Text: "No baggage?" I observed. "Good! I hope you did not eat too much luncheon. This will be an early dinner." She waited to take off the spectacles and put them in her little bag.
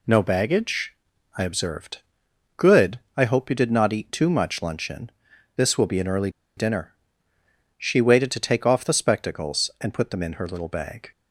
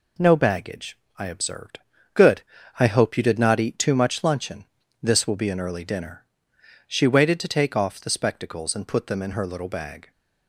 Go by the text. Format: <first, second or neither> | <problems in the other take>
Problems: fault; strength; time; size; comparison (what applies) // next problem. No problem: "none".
second | pauses between "early" and "dinner"; slight; at 6.2 s; 0.27 s long